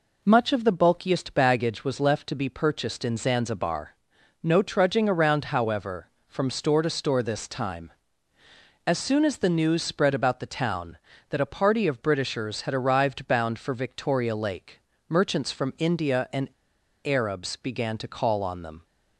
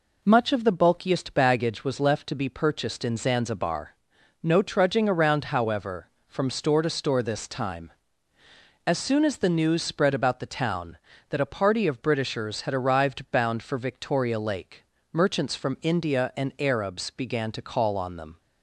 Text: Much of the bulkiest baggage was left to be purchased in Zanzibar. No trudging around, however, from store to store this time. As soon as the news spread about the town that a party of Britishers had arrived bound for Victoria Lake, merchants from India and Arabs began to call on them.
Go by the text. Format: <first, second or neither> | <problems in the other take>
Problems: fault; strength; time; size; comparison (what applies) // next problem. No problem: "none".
second | pauses between "and" and "Arabs"; noticeable; at 16.5 s; 0.53 s long